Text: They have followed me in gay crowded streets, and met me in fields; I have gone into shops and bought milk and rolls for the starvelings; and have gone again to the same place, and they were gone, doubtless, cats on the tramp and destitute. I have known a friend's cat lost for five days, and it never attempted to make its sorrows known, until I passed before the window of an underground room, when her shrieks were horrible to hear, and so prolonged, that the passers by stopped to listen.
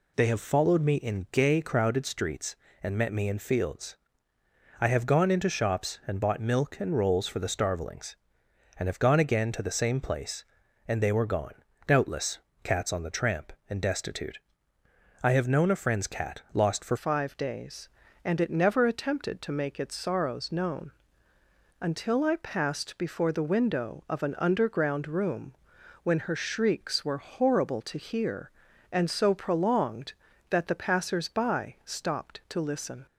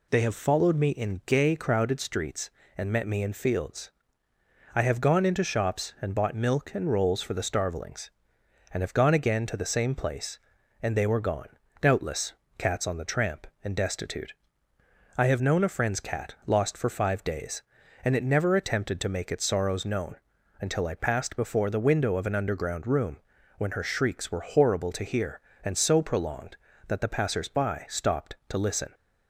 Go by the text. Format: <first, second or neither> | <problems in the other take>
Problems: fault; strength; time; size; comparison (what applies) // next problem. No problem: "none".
second | changes voice at "five"; from 16.9 s on; 16.1 s long